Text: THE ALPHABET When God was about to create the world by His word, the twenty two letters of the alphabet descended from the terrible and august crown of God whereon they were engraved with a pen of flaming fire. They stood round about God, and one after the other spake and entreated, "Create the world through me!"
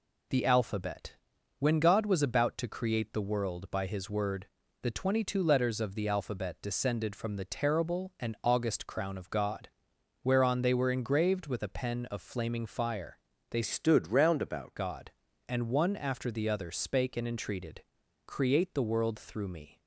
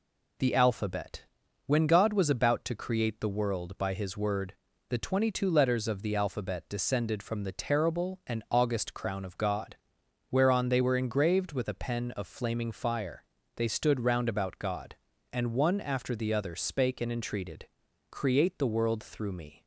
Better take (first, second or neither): second